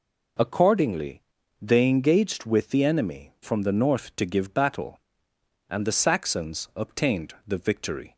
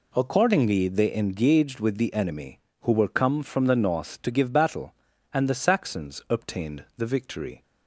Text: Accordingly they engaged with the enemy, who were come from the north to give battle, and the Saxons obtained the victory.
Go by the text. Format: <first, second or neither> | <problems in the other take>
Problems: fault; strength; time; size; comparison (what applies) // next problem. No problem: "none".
second | pauses between "Accordingly" and "they"; at 1.2 s; 0.38 s long // skips "who were come"; at 3.3 s